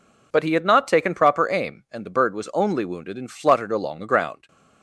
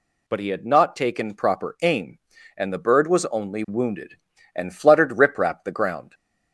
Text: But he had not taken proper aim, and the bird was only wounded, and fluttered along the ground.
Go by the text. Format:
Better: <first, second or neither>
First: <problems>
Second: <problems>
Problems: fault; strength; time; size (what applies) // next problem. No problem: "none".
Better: first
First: none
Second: says "riprap" for "along"; at 5.1 s